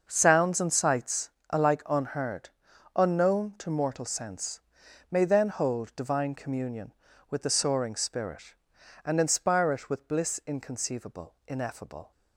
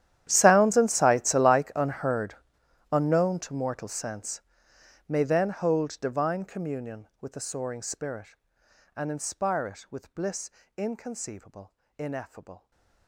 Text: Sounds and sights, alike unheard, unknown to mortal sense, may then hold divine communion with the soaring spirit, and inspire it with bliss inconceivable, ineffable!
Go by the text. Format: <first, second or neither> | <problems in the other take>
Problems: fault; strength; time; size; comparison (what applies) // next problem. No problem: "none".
first | gets quieter; strong; throughout; 23.5 dB // starts louder than the rest; strong; until 1.2 s; 11 dB; noticeable in the first // pauses between "bliss" and "inconceivable"; slight; at 10.4 s; 0.28 s long // stays silent after the last word; slight; from 12.5 s on; 0.5 s long